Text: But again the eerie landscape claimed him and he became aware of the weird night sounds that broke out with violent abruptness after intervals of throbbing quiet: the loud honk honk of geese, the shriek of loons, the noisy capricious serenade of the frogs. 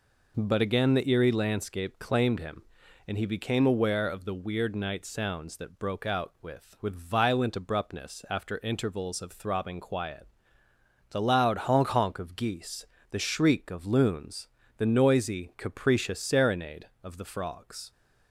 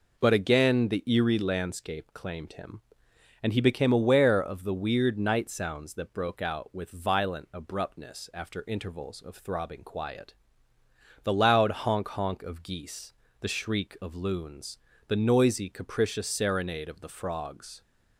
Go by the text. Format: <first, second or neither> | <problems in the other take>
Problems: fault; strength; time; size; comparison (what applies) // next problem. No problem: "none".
second | says "with" twice; at 6.8 s